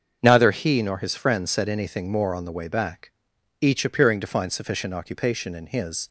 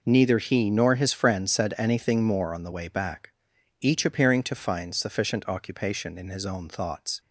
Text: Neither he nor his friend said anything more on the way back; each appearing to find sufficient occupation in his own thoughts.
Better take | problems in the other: second | starts louder than the rest; until 1.2 s; 6.5 dB // stops before "own thoughts"; at 6.0 s

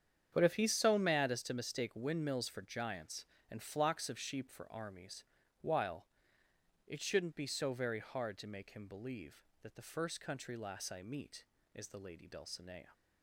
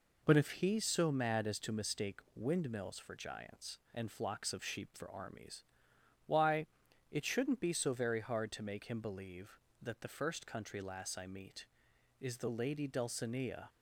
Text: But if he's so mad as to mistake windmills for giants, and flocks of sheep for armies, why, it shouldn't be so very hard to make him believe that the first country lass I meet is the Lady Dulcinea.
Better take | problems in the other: second | starts louder than the rest; strong; until 1.3 s; 8.5 dB // says "while" for "why"; at 5.6 s

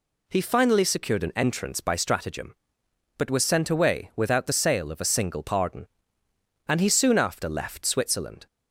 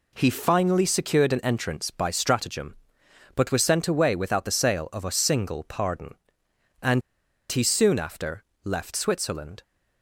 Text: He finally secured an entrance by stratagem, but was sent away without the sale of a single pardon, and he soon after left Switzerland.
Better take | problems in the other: first | pauses between "and" and "he"; noticeable; at 7.0 s; 0.49 s long // pauses between "after" and "left"; slight; at 8.4 s; 0.18 s long

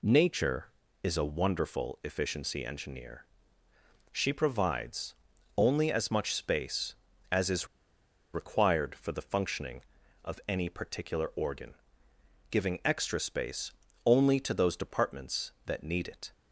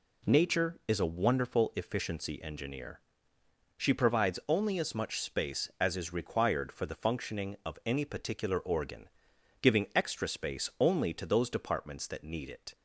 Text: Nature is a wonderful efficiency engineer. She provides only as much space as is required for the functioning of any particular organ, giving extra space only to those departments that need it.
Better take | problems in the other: second | pauses between "provides" and "only"; at 5.1 s; 0.42 s long // pauses between "is" and "required"; noticeable; at 7.6 s; 0.66 s long // pauses between "space" and "only"; slight; at 13.7 s; 0.32 s long

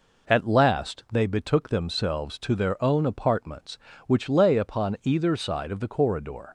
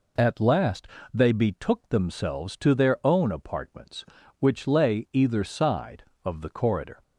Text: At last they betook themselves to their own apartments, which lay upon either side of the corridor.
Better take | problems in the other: first | pauses between "last" and "they"; slight; at 0.8 s; 0.26 s long // skips "upon"; at 5.0 s

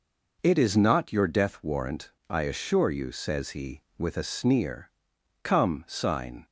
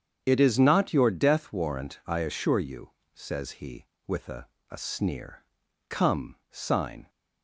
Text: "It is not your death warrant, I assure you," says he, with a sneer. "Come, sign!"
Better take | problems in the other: first | starts louder than the rest; strong; until 1.2 s; 8 dB // says "a" twice; at 4.7 s

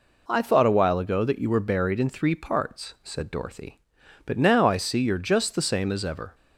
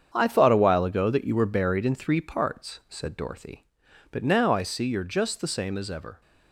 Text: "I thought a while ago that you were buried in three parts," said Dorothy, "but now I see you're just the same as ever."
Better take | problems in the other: first | gets quieter; strong; throughout; 9.5 dB

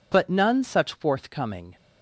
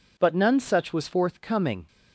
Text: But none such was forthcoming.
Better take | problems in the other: second | skips "was"; at 0.9 s

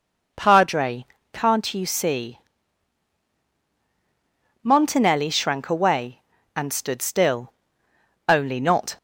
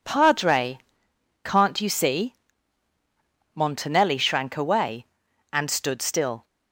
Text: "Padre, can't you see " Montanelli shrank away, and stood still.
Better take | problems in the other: second | goes on to say "Only not"; noticeable; from 8.2 s on; 0.70 s long

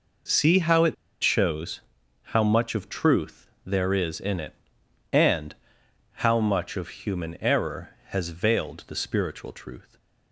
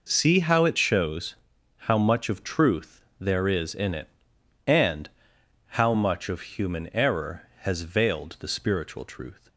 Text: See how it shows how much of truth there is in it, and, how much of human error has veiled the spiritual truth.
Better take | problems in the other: second | pauses between "it" and "shows"; slight; at 0.9 s; 0.27 s long // pauses between "shows" and "how"; at 1.8 s; 0.44 s long; also in the second // pauses between "truth" and "there"; slight; at 3.4 s; 0.16 s long; slight in the second

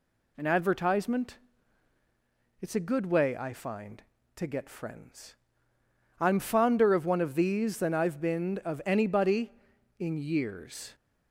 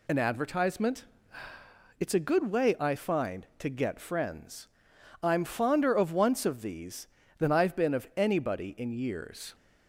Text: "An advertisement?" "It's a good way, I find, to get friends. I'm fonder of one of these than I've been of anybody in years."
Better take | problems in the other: first | says "once" for "one"; at 6.1 s

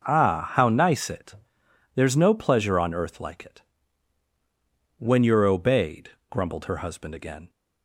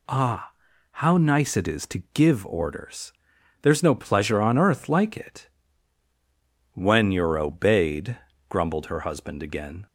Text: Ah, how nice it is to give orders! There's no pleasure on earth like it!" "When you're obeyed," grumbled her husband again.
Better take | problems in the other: second | skips "is to give orders"; at 1.6 s

